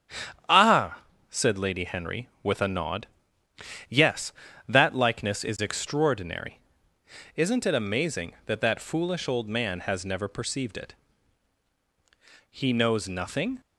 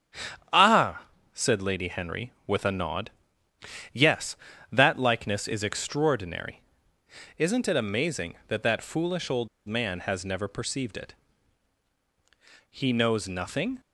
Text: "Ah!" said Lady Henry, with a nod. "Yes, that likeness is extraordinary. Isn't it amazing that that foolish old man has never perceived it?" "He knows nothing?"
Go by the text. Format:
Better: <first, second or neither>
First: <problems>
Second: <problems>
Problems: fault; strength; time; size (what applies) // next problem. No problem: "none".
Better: first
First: starts louder than the rest; strong; until 1.7 s; 9.5 dB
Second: starts louder than the rest; strong; until 1.7 s; 9 dB // pauses between "old" and "man"; slight; at 9.4 s; 0.20 s long